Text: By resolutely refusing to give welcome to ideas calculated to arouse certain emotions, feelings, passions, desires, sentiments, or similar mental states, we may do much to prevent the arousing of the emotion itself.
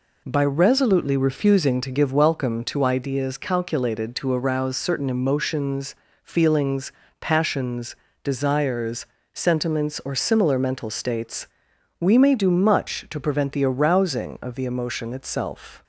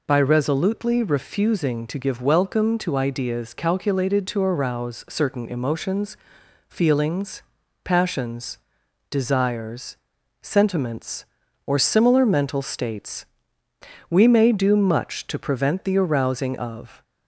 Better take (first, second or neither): first